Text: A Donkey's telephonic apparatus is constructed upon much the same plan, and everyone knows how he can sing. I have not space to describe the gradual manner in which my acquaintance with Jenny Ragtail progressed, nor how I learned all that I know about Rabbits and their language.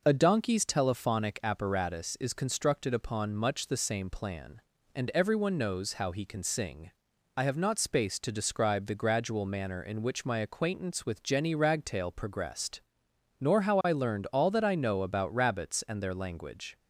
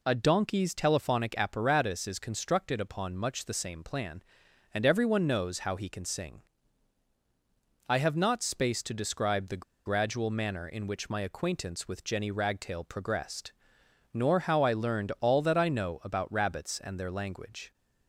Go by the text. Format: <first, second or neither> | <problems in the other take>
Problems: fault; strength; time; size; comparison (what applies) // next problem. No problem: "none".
first | pauses between "the" and "gradual"; slight; at 9.6 s; 0.24 s long